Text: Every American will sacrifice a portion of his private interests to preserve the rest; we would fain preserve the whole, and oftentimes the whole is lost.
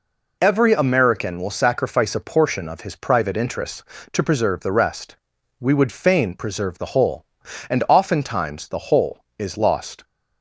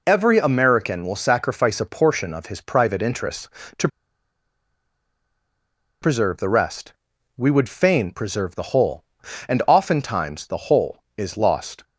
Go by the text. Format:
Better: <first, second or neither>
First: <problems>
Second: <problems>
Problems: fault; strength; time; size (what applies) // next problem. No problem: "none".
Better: first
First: none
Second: pauses between "to" and "preserve"; strong; at 3.8 s; 2.1 s long